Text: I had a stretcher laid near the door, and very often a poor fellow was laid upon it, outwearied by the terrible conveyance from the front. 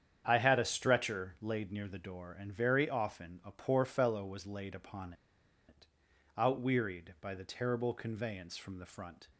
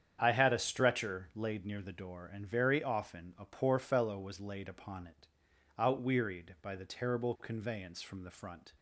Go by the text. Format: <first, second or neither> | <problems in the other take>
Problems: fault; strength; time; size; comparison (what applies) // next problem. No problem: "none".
second | starts louder than the rest; strong; until 1.2 s; 8.5 dB; strong in the second // pauses between "upon" and "it"; noticeable; at 5.1 s; 0.55 s long